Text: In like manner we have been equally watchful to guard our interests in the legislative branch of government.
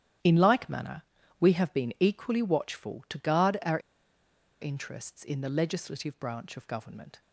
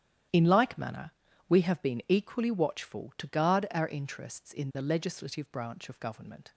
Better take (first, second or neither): second